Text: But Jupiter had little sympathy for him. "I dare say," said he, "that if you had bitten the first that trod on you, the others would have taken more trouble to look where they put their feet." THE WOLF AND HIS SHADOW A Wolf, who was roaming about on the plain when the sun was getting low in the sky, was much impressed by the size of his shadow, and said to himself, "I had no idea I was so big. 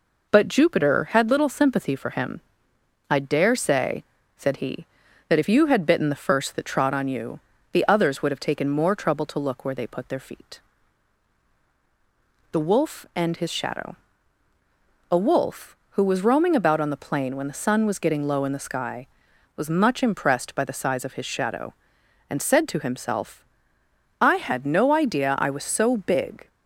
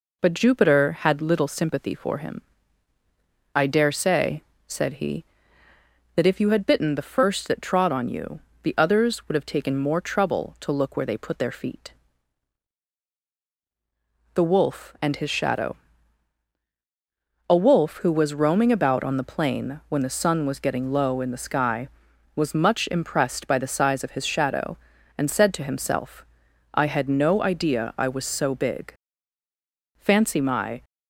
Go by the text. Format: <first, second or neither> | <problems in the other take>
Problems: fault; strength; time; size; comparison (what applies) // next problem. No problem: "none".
first | pauses between "SHADOW" and "A"; strong; at 15.7 s; 1.7 s long; also in the first // goes on to say "Fancy my"; noticeable; from 29.9 s on; 0.86 s long